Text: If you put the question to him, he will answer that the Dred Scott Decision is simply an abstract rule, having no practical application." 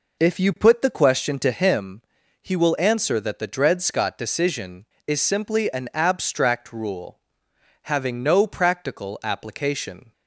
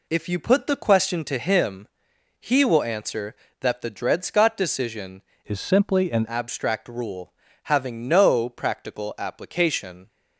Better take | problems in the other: first | changes voice from "is" to "an"; from 5.4 to 6.2 s; 0.8 s long

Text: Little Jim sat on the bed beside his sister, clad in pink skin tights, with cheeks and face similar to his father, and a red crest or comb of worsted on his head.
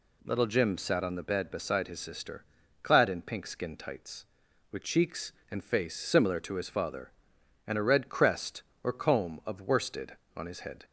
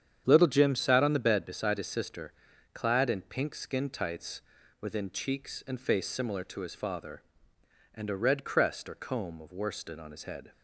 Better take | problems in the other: first | starts louder than the rest; strong; until 1.2 s; 8.5 dB // says "within" for "with"; at 4.8 s

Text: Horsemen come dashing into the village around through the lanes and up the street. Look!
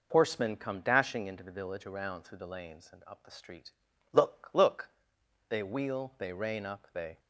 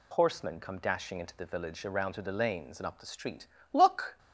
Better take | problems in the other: second | goes on to say "Look they wheel they rein up they"; strong; from 4.5 s on; 2.6 s long

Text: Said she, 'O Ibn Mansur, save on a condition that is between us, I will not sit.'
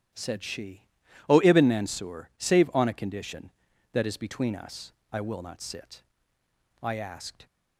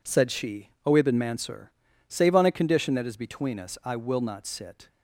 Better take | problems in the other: second | starts louder than the rest; strong; until 1.6 s; 12.5 dB // goes on to say "I asked"; noticeable; from 6.8 s on; 0.64 s long

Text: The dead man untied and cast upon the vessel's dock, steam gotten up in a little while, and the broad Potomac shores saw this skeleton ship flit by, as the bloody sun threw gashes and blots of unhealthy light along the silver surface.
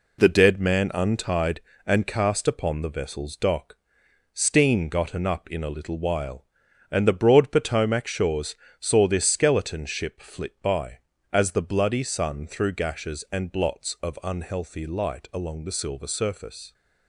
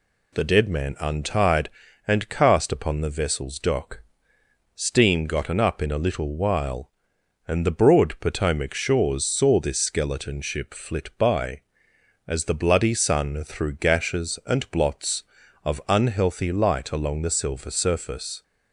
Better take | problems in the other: second | gets quieter; noticeable; throughout; 6 dB // pauses between "shores" and "saw"; slight; at 8.5 s; 0.28 s long

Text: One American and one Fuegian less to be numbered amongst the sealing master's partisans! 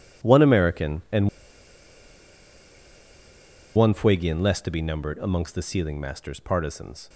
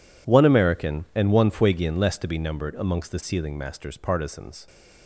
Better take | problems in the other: second | pauses between "and" and "one"; strong; at 1.2 s; 2.4 s long

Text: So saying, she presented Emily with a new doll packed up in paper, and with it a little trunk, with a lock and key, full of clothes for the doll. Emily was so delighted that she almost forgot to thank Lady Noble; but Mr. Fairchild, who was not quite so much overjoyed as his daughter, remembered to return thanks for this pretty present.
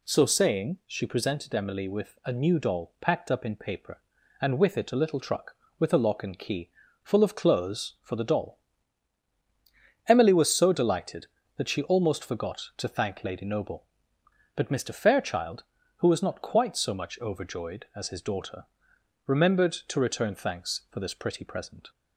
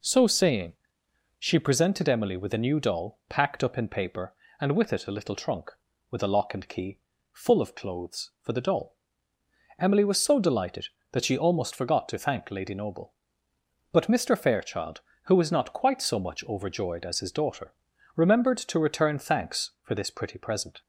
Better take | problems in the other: second | says "truck" for "trunk"; at 5.2 s

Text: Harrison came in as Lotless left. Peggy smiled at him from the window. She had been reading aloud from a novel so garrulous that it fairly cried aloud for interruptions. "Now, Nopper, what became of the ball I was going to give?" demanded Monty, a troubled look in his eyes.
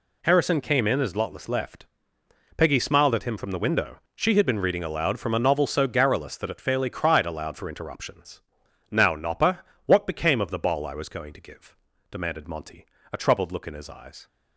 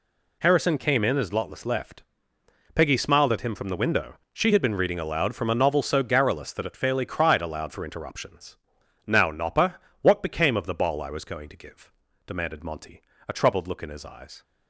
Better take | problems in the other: neither | none

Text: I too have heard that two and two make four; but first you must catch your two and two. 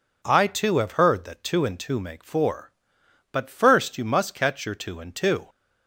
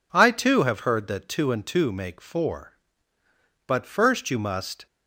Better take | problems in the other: first | stops before "catch your two and two"; at 4.8 s

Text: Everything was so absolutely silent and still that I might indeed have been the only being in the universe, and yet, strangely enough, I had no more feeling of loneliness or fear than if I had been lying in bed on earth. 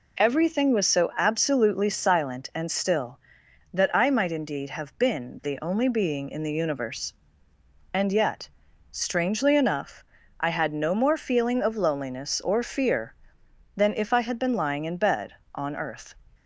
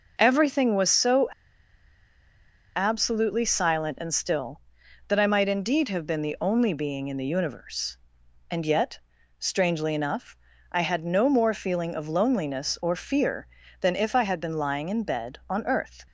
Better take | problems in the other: first | pauses between "so" and "absolutely"; strong; at 1.2 s; 1.4 s long

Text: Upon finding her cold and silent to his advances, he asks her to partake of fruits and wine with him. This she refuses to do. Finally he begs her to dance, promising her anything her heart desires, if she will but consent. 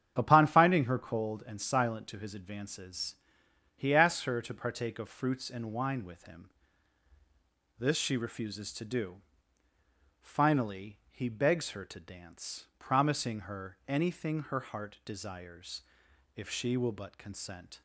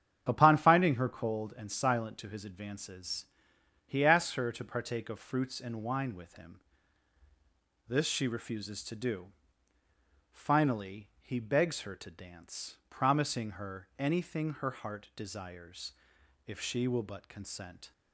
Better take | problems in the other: neither | starts louder than the rest; strong; the same in both

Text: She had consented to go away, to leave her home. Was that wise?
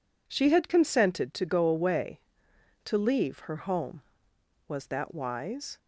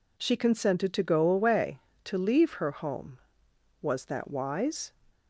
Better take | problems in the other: first | skips "had"; at 0.3 s

